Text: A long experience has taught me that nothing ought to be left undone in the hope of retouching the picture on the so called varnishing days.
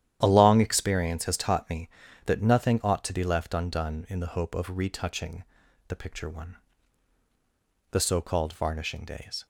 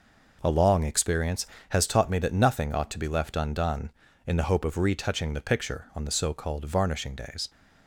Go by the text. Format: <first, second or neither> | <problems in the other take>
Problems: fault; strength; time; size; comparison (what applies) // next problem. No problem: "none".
second | starts louder than the rest; strong; until 1.2 s; 11 dB // pauses between "retouching" and "the"; at 5.4 s; 0.44 s long // says "one" for "on"; at 6.2 s